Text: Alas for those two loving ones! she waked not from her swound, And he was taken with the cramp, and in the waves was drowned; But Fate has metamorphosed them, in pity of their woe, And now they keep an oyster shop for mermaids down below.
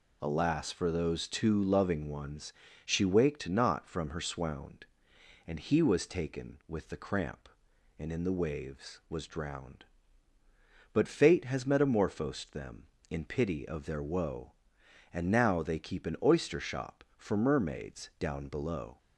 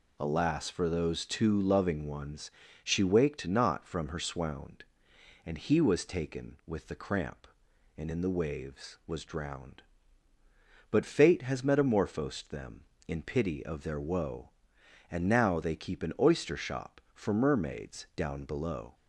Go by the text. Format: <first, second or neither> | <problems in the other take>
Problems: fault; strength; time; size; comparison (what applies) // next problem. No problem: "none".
neither | none